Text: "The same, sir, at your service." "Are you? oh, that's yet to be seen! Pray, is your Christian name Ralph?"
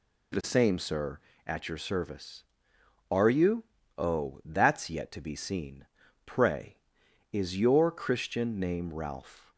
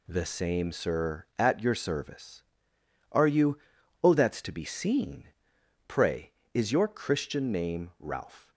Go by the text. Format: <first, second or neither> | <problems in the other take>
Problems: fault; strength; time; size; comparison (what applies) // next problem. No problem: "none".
first | skips "yet"; at 4.4 s